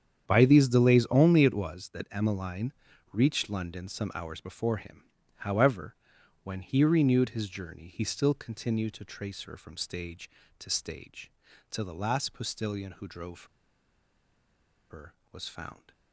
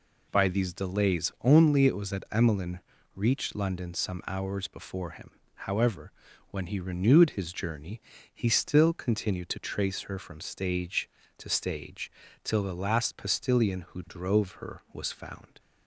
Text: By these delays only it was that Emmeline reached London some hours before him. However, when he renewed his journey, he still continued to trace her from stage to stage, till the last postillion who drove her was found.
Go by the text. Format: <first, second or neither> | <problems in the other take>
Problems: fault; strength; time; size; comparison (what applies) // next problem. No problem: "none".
second | starts louder than the rest; strong; until 1.2 s; 8.5 dB // pauses between "Emmeline" and "reached"; at 2.7 s; 0.40 s long; slight in the second // pauses between "drove" and "her"; strong; at 13.4 s; 1.4 s long